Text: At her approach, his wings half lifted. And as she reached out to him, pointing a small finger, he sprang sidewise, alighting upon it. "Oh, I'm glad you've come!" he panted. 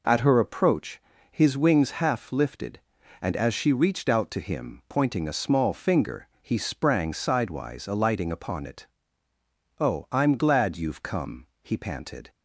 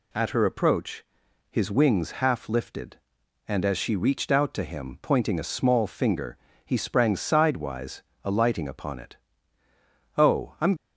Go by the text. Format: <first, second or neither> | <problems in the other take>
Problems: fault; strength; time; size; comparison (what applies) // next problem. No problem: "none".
first | stops before "glad you've come he panted"; at 10.7 s